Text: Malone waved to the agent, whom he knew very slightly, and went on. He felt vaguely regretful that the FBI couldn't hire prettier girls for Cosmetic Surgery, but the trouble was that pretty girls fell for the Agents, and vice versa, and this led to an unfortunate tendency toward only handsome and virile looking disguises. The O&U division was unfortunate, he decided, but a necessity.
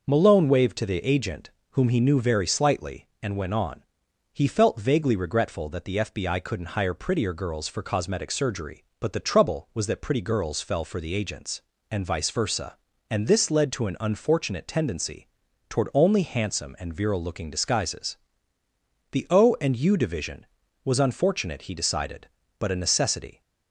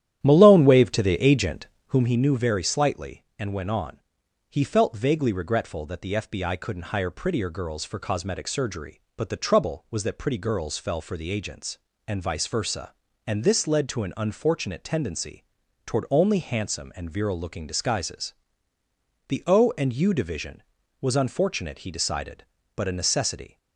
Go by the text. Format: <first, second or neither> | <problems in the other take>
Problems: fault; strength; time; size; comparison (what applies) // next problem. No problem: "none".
first | starts louder than the rest; strong; until 2.1 s; 11 dB // pauses between "tendency" and "toward"; at 15.4 s; 0.44 s long; also in the first